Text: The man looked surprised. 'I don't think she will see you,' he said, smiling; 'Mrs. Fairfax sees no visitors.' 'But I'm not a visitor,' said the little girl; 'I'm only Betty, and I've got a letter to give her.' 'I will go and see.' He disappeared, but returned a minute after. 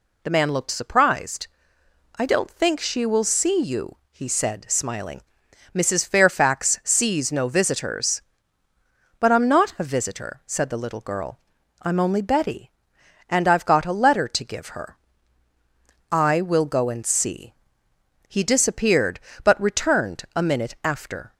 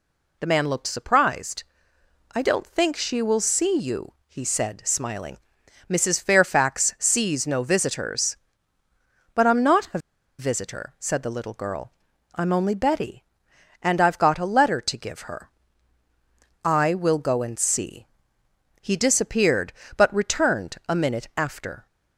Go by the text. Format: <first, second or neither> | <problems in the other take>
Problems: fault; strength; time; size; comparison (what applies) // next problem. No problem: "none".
first | pauses between "a" and "visitor"; at 9.9 s; 0.40 s long